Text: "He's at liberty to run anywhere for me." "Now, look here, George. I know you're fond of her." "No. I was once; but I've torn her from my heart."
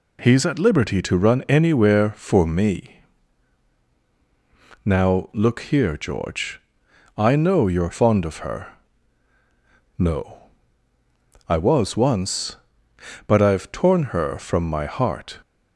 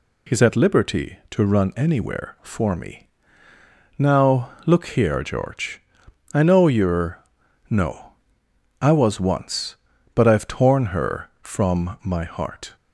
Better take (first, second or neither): first